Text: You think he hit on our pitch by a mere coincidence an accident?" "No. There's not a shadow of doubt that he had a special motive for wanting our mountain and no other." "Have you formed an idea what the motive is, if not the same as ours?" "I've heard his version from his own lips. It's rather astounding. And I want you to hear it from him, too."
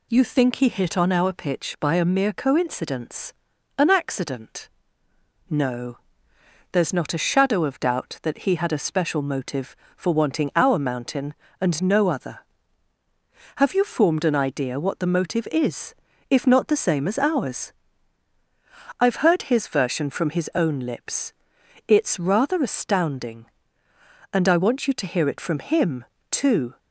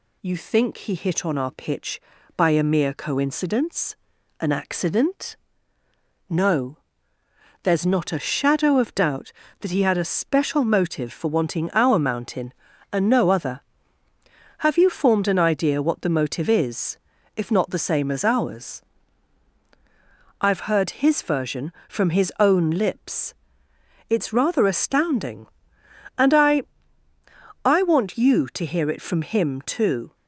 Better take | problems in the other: first | pauses between "coincidence" and "an"; noticeable; at 3.9 s; 0.46 s long; noticeable in the first // says "I" twice; at 27.6 s

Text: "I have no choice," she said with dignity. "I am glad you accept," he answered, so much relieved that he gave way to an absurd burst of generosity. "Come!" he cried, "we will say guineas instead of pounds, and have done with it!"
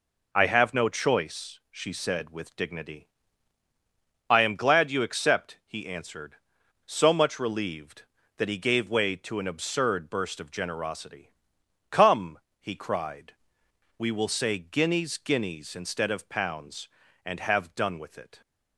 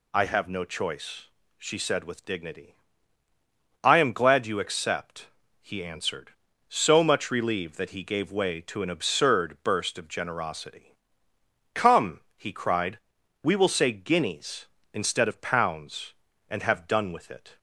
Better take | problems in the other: second | says "guineas" twice; at 15.1 s

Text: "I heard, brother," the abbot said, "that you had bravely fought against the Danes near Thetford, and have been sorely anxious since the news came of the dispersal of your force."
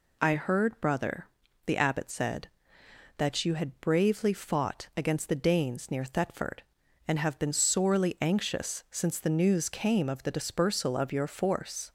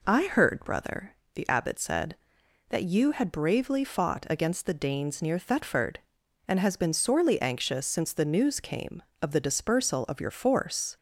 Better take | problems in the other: first | says "has" for "have"; at 6.5 s

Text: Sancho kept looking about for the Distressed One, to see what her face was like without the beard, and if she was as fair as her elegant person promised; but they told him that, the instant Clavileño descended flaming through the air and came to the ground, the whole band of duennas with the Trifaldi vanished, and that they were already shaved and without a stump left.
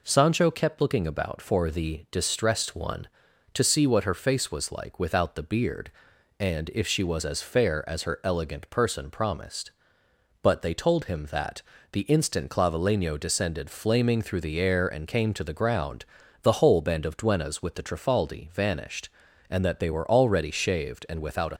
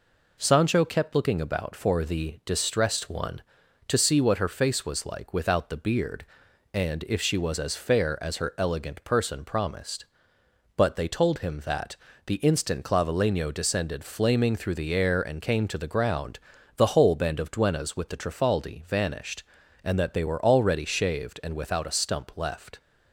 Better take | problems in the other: second | stops before "stump left"; at 21.5 s

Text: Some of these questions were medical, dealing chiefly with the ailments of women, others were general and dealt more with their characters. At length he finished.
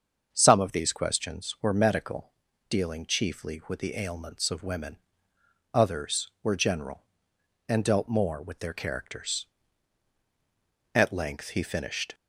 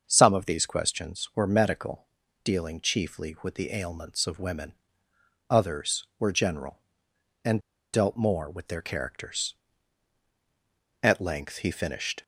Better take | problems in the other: first | starts louder than the rest; until 1.0 s; 6.5 dB; also in the first // pauses between "and" and "dealt"; slight; at 7.6 s; 0.33 s long

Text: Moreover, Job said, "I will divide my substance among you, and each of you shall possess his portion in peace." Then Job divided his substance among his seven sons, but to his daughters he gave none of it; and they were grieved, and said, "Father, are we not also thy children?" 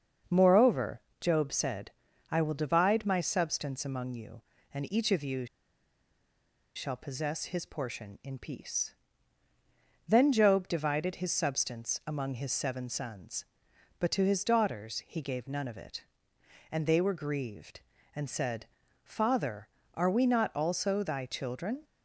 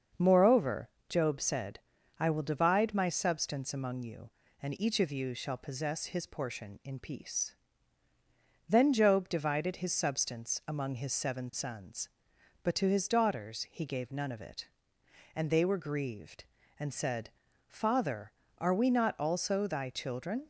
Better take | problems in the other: second | starts louder than the rest; until 1.5 s; 6.5 dB; also in the second // pauses between "you" and "shall"; strong; at 5.4 s; 1.2 s long

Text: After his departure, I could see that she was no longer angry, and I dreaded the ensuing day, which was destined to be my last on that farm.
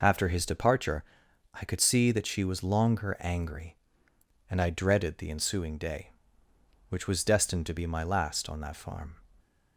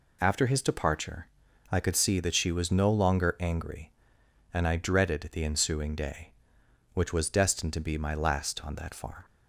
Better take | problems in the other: second | skips "no"; at 2.6 s

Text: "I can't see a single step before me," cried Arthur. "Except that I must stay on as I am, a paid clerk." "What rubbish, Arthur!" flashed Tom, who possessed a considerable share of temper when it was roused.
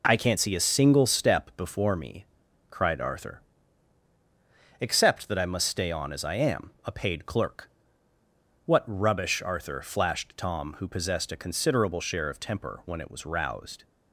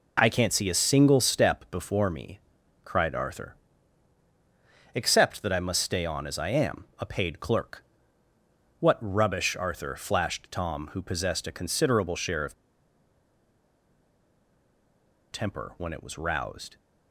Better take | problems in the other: first | pauses between "of" and "temper"; strong; at 12.5 s; 2.7 s long

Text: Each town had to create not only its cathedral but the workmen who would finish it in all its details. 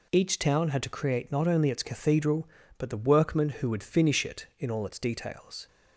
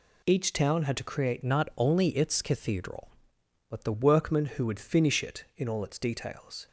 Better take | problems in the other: first | changes voice from "not" to "the"; from 1.4 to 3.9 s; 2.5 s long

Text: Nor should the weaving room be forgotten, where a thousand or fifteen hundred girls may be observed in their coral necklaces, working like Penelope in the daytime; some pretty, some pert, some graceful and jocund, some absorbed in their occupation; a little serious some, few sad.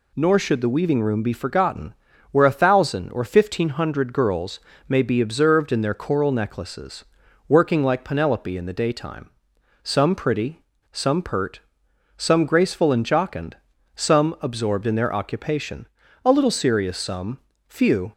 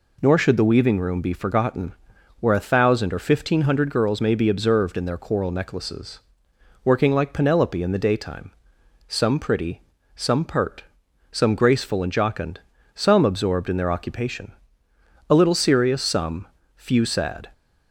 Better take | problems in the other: second | pauses between "girls" and "may"; slight; at 4.5 s; 0.28 s long // stops before "sad"; at 18.1 s

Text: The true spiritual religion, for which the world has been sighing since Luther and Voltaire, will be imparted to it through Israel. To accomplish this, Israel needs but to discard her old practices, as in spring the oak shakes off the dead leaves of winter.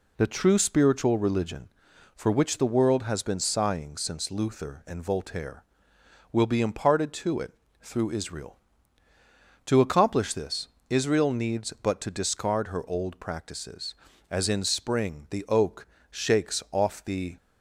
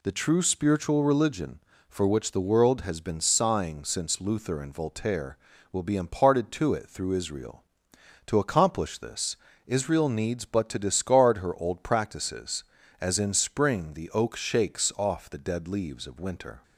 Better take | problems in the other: second | pauses between "it" and "through"; slight; at 7.5 s; 0.28 s long // pauses between "oak" and "shakes"; slight; at 15.8 s; 0.26 s long // stops before "dead leaves of winter"; at 17.3 s

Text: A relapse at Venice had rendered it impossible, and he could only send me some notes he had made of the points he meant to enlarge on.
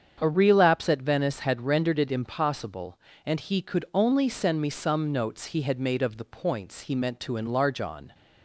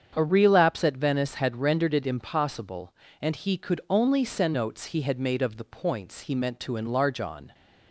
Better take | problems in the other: first | starts louder than the rest; strong; until 1.1 s; 7.5 dB; strong in the first // skips "me some"; at 4.5 s

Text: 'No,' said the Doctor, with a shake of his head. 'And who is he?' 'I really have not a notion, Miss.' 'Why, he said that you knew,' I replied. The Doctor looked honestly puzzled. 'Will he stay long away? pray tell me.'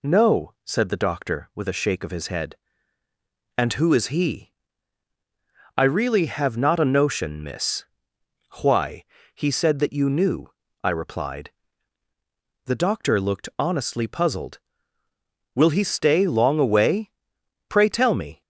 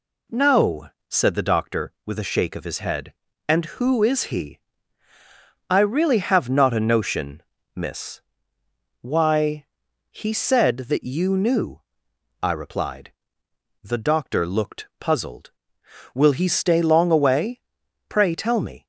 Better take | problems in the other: first | skips "honestly"; at 14.9 s

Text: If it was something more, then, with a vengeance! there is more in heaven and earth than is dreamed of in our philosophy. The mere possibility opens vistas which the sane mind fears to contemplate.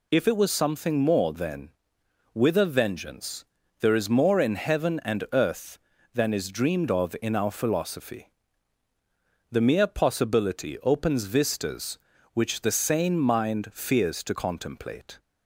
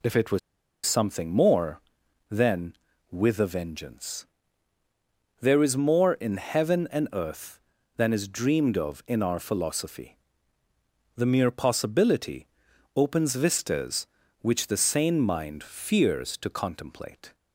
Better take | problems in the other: first | pauses between "was" and "something"; noticeable; at 0.3 s; 0.46 s long // pauses between "possibility" and "opens"; noticeable; at 12.4 s; 0.50 s long

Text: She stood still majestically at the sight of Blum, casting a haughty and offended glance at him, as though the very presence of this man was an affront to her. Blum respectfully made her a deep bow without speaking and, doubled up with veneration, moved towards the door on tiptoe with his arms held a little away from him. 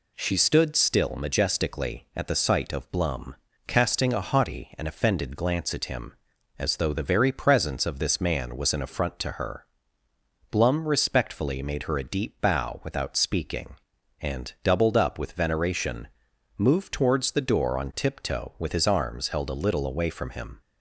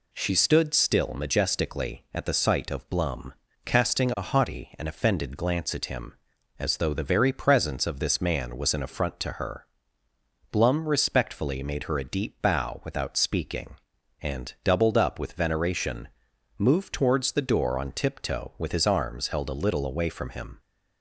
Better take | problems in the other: neither | none

